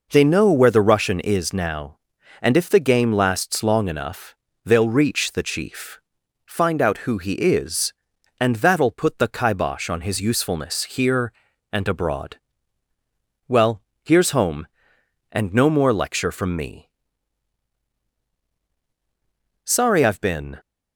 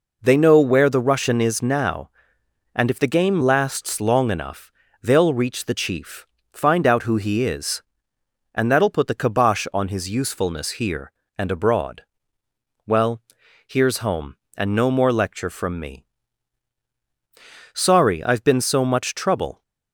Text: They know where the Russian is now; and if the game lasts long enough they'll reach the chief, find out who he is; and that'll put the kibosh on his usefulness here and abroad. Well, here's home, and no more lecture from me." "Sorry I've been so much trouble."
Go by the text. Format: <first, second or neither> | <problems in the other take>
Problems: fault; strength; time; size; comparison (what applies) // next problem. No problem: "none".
second | pauses between "enough" and "they'll"; slight; at 4.3 s; 0.28 s long; slight in the second // stops before "so much trouble"; at 20.5 s